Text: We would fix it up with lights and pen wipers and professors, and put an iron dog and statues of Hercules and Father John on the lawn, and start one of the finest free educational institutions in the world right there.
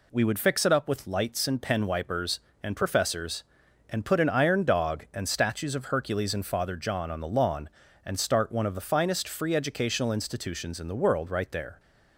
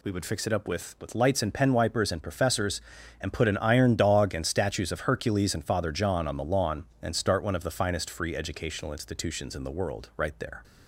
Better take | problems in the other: first | says "with" twice; at 1.0 s

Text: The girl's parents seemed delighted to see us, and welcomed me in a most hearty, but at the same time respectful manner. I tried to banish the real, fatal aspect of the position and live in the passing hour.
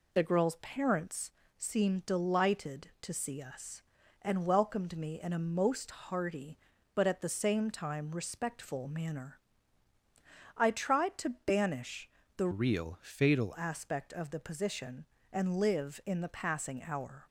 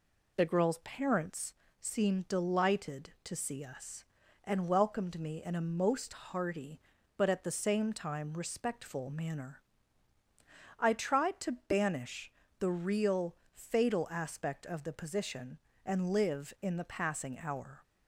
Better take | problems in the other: second | pauses between "parents" and "seemed"; slight; at 1.3 s; 0.26 s long; slight in the second // pauses between "banish" and "the"; slight; at 12.0 s; 0.26 s long; slight in the second // changes voice from "real" to "fatal"; from 12.5 to 13.5 s; 1.0 s long

